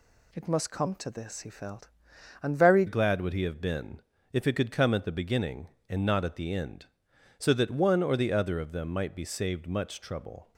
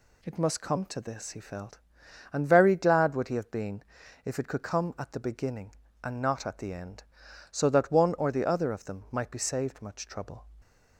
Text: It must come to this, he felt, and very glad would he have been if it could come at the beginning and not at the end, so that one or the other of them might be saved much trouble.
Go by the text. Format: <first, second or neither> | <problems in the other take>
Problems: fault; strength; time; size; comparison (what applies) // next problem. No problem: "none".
second | changes voice at "glad"; from 2.8 s on; 7.7 s long // pauses between "been" and "if"; slight; at 4.0 s; 0.30 s long; also in the second